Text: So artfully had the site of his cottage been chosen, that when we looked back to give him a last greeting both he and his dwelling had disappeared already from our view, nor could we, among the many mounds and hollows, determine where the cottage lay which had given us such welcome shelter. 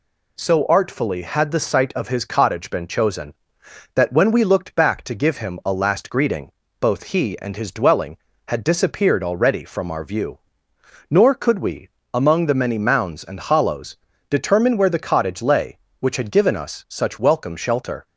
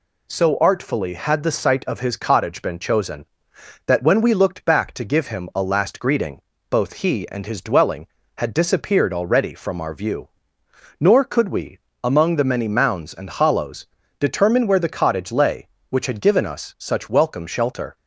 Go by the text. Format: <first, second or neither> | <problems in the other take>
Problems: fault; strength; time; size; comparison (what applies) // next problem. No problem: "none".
neither | pauses between "greeting" and "both"; slight; the same in both